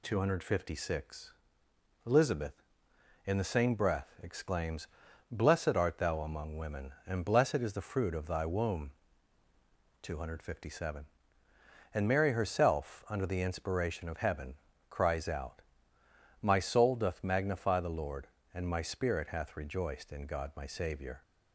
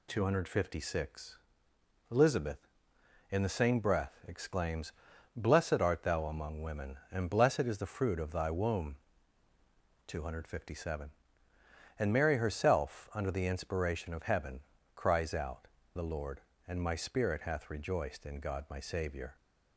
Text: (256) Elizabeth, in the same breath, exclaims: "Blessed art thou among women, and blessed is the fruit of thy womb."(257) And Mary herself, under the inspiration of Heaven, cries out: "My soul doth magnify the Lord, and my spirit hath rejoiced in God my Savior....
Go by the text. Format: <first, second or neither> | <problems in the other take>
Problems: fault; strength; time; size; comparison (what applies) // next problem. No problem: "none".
first | skips "My soul doth magnify"; at 15.8 s